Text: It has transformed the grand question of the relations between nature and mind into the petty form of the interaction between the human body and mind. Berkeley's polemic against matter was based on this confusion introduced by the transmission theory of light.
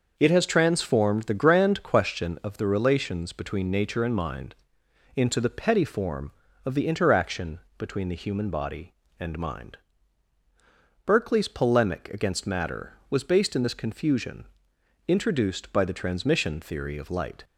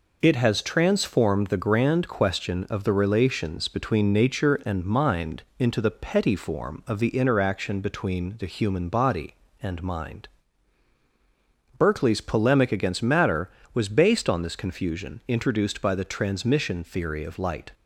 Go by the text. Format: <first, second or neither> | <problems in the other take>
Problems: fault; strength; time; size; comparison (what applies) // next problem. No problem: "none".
second | starts louder than the rest; noticeable; until 1.1 s; 6 dB // pauses between "mind" and "into"; noticeable; at 4.5 s; 0.60 s long; slight in the second // pauses between "interaction" and "between"; slight; at 7.5 s; 0.18 s long // says "in" for "on"; at 13.5 s // pauses between "confusion" and "introduced"; noticeable; at 14.4 s; 0.62 s long